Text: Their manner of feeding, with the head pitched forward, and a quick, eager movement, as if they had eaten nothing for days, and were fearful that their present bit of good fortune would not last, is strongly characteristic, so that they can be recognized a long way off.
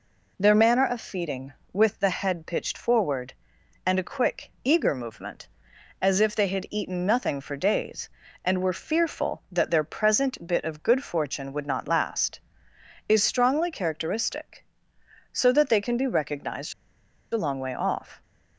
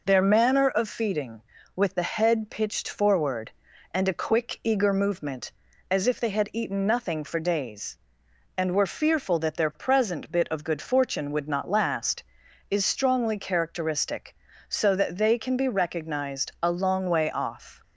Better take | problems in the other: second | pauses between "recognized" and "a"; noticeable; at 16.7 s; 0.58 s long

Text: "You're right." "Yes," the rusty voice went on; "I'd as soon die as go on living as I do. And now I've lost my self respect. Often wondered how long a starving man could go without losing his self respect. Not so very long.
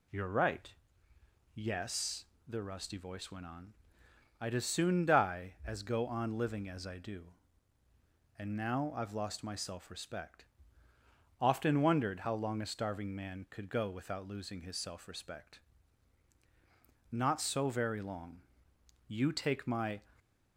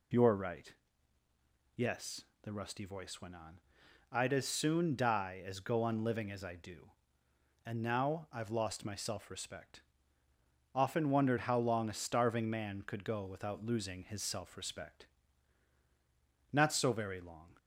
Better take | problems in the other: second | goes on to say "You take my"; noticeable; from 19.0 s on; 0.94 s long

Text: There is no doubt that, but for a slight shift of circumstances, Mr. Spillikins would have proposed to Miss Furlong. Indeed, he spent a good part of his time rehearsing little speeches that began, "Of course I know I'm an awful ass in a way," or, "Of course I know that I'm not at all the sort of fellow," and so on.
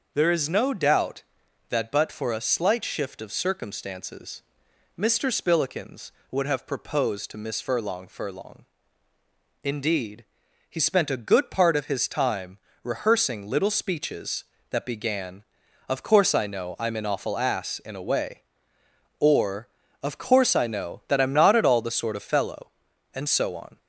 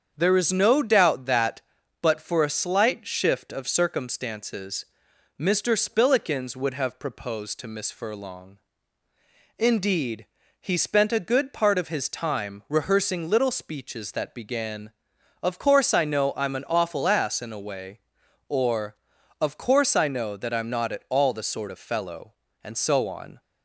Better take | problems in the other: second | starts louder than the rest; until 1.1 s; 6.5 dB; strong in the second // says "Furlong" twice; at 8.0 s // pauses between "time" and "rehearsing"; slight; at 12.5 s; 0.26 s long

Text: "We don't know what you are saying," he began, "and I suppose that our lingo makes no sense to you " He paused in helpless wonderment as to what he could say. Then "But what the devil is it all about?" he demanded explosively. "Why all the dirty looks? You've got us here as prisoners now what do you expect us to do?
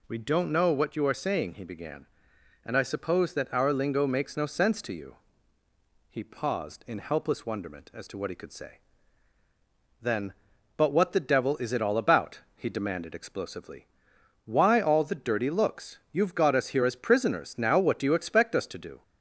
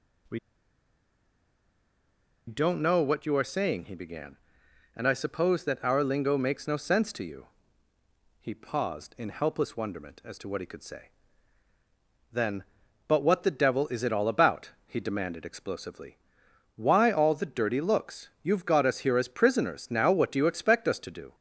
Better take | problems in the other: first | pauses between "We" and "don't"; strong; at 0.3 s; 2.0 s long

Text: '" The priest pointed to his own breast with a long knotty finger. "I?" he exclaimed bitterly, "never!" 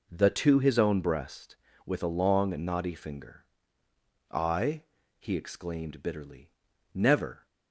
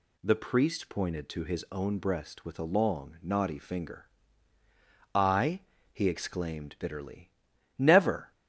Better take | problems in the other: second | skips "priest pointed"; at 0.3 s

